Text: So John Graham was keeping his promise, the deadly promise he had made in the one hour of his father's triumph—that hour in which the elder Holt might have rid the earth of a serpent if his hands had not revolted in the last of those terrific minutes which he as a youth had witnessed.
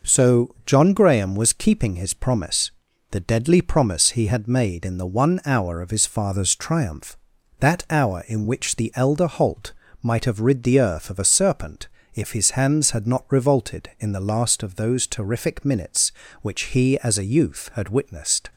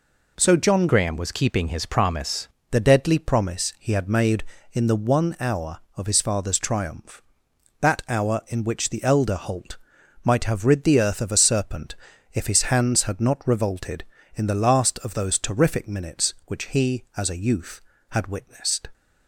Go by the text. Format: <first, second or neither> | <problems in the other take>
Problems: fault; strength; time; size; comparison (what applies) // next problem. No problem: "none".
first | changes voice from "Graham" to "promise"; from 0.8 to 2.4 s; 1.6 s long // pauses between "Holt" and "might"; noticeable; at 9.7 s; 0.48 s long; slight in the first // pauses between "serpent" and "if"; at 11.9 s; 0.38 s long; slight in the first